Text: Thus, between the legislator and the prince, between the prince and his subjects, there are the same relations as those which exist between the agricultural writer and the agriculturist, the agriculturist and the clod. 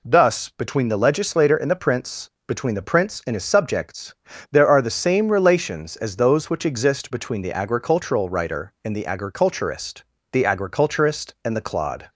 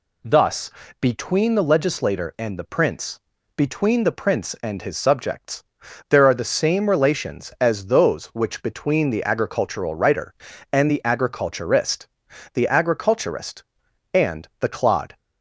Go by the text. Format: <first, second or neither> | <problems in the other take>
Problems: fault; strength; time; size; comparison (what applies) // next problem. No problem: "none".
first | skips "exist"; at 8.6 s